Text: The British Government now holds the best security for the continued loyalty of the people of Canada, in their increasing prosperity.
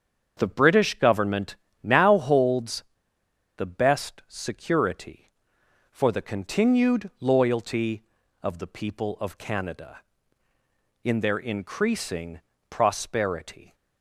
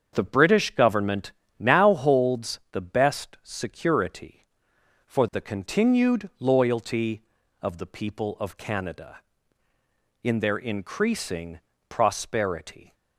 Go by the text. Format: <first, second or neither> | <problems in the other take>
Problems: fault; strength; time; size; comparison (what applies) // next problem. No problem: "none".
second | starts louder than the rest; strong; until 1.3 s; 7 dB; strong in the second // pauses between "Government" and "now"; slight; at 1.5 s; 0.26 s long; slight in the second // pauses between "holds" and "the"; noticeable; at 2.8 s; 0.73 s long // pauses between "increasing" and "prosperity"; slight; at 12.4 s; 0.28 s long; slight in the second